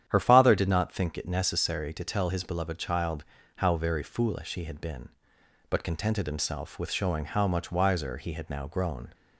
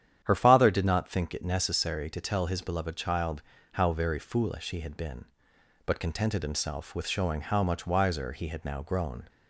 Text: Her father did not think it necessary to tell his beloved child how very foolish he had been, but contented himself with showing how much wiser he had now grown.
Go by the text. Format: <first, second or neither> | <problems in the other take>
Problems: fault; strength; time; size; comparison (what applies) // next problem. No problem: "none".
neither | starts louder than the rest; strong; the same in both // pauses between "child" and "how"; slight; the same in both